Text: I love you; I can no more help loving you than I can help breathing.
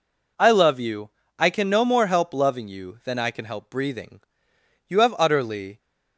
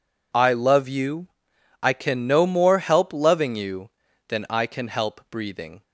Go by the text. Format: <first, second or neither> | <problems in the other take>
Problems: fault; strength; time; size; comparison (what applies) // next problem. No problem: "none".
second | goes on to say "You have utterly"; noticeable; from 4.8 s on; 0.90 s long